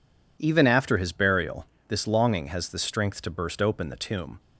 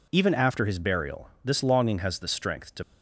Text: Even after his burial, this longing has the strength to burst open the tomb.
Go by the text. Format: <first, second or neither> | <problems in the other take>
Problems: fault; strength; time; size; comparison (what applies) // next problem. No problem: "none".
first | stops before "burst open the tomb"; at 2.8 s